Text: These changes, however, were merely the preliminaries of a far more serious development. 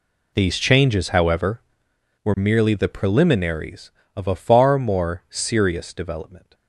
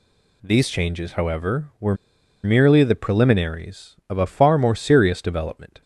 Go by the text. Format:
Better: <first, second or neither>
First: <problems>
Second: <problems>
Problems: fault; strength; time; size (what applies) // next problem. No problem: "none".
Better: first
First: none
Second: pauses between "were" and "merely"; noticeable; at 1.9 s; 0.49 s long